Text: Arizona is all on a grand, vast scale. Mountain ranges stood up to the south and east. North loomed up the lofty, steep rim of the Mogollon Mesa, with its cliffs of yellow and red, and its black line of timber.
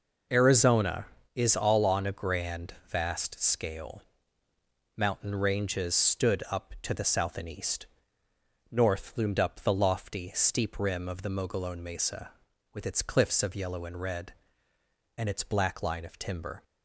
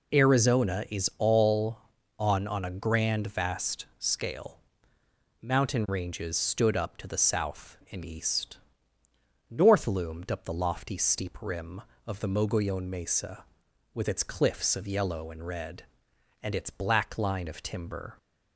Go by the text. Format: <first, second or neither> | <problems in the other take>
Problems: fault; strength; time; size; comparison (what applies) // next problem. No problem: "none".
first | says "on" twice; at 2.4 s